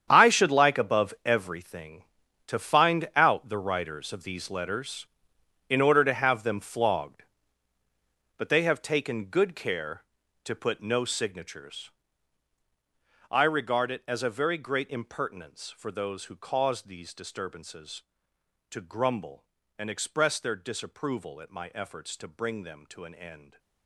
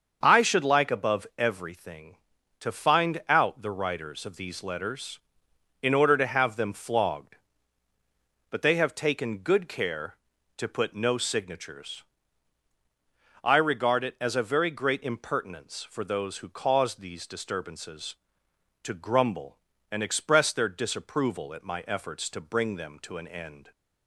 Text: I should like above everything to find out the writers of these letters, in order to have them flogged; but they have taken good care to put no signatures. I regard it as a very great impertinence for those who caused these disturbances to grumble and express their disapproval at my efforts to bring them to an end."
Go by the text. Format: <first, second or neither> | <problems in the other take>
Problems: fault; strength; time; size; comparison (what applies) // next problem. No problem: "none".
second | gets quieter; strong; throughout; 14 dB // starts louder than the rest; strong; until 1.1 s; 8.5 dB; also in the second